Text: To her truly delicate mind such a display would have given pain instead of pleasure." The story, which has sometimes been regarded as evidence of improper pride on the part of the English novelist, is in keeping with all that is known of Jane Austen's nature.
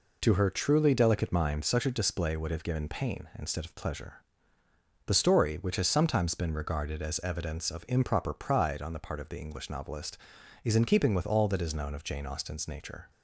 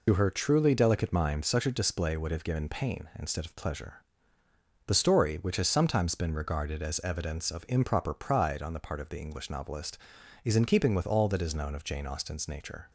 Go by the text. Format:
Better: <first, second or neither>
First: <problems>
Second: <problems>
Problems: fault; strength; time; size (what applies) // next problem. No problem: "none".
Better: first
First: none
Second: loses the start of "To"; at 0.0 s; 55 ms